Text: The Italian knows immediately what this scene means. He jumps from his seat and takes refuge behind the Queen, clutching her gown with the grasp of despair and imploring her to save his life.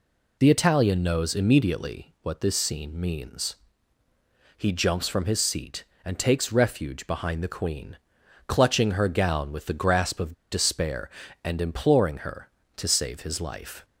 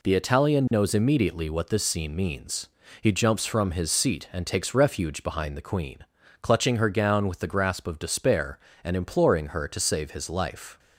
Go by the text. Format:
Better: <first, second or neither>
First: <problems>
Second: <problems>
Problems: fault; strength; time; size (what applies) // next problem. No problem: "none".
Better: second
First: pauses between "of" and "despair"; slight; at 10.3 s; 0.18 s long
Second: none